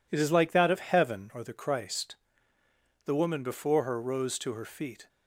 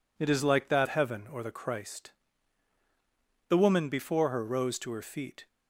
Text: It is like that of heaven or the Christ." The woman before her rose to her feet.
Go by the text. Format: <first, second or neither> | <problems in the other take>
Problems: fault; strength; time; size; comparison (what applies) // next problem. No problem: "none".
first | skips "of"; at 0.8 s